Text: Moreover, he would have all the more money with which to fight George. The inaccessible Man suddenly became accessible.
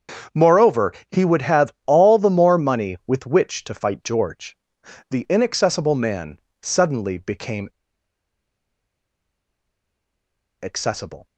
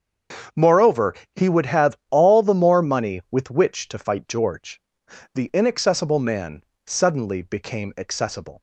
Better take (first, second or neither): second